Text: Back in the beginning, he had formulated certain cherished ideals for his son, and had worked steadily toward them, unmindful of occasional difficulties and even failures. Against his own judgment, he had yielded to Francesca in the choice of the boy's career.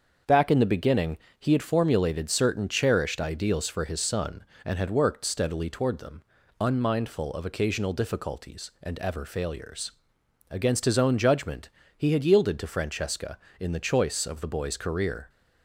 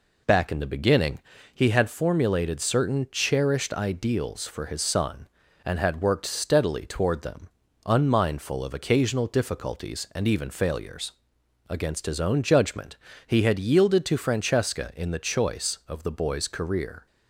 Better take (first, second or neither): second